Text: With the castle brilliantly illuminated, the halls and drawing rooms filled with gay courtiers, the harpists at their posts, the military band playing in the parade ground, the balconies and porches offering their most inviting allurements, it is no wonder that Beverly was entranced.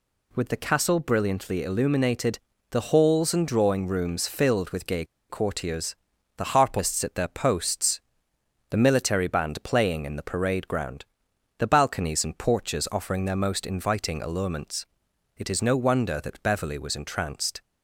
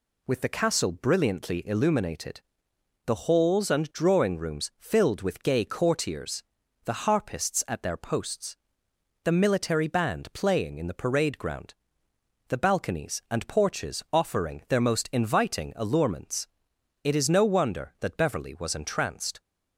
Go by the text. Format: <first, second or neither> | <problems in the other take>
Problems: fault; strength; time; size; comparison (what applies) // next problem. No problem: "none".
second | pauses between "gay" and "courtiers"; slight; at 5.0 s; 0.26 s long